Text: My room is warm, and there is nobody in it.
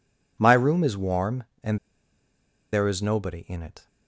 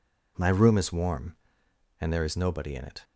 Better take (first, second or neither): second